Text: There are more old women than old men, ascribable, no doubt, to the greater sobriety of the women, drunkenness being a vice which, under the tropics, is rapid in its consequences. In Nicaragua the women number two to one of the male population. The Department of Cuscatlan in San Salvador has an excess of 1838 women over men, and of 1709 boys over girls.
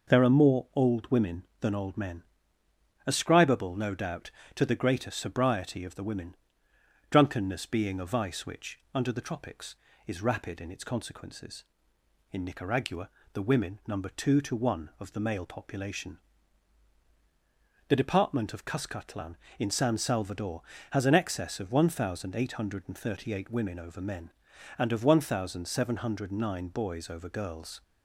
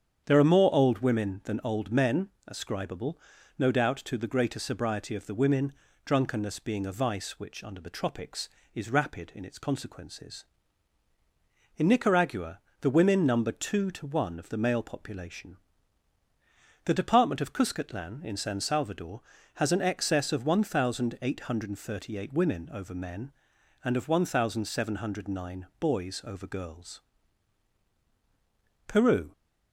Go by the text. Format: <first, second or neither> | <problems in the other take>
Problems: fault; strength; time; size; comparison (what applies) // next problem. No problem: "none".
first | starts louder than the rest; strong; until 1.2 s; 8.5 dB // pauses between "Nicaragua" and "the"; slight; at 12.5 s; 0.22 s long; slight in the first // goes on to say "Peru"; slight; from 28.8 s on; 0.46 s long